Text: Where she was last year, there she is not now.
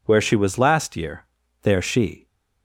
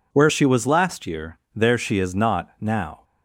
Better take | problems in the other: second | stops before "is not now"; at 2.2 s

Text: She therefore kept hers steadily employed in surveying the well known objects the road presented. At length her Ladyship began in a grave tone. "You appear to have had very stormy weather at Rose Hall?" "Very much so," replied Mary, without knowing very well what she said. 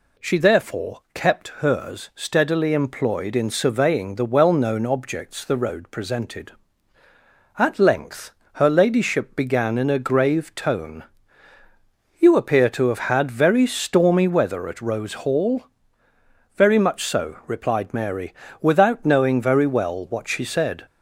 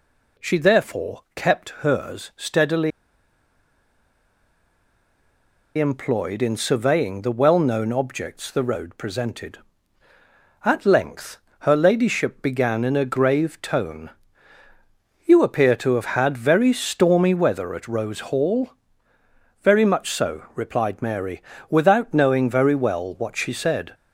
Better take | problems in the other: first | pauses between "steadily" and "employed"; strong; at 2.9 s; 2.8 s long // pauses between "length" and "her"; slight; at 11.3 s; 0.22 s long; slight in the first

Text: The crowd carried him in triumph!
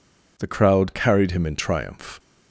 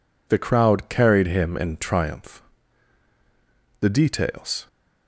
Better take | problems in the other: first | goes on to say "The details"; noticeable; from 3.7 s on; 0.88 s long

